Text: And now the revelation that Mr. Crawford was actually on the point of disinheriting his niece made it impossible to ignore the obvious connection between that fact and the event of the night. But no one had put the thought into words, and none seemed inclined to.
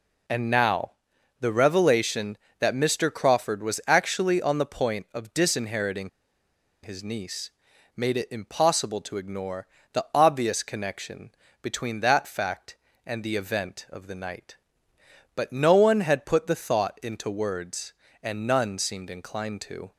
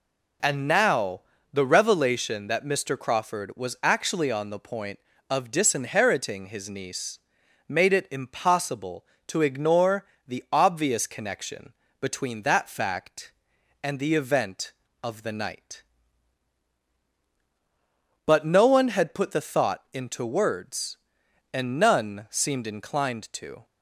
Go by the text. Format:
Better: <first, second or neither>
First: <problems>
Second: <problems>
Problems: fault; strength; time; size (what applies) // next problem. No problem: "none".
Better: second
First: pauses between "now" and "the"; noticeable; at 0.9 s; 0.48 s long // pauses between "disinheriting" and "his"; noticeable; at 6.0 s; 0.74 s long // pauses between "niece" and "made"; at 7.5 s; 0.44 s long // pauses between "ignore" and "the"; slight; at 9.6 s; 0.26 s long // pauses between "connection" and "between"; slight; at 11.3 s; 0.30 s long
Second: pauses between "now" and "the"; slight; at 1.2 s; 0.32 s long // pauses between "niece" and "made"; noticeable; at 7.1 s; 0.50 s long // pauses between "ignore" and "the"; slight; at 10.0 s; 0.22 s long // pauses between "connection" and "between"; slight; at 11.7 s; 0.28 s long